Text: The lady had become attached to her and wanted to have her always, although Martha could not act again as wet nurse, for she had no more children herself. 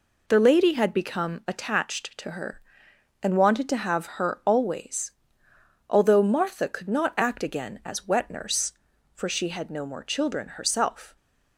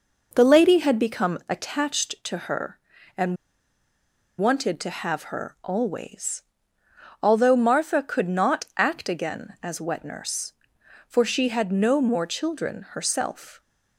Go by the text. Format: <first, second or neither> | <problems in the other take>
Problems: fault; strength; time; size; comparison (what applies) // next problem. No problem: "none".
first | pauses between "and" and "wanted"; at 3.3 s; 1.0 s long